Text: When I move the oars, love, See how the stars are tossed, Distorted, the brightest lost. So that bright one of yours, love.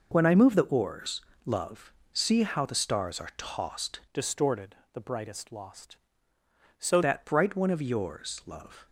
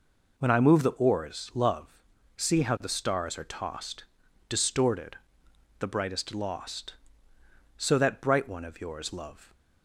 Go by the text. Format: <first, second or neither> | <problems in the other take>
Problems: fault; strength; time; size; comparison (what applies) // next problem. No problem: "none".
second | changes voice from "Distorted" to "So"; from 4.1 to 6.9 s; 2.8 s long